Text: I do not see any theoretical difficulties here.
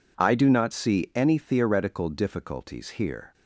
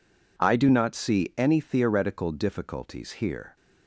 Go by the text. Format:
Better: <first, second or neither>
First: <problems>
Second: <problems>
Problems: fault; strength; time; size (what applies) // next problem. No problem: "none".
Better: neither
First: none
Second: none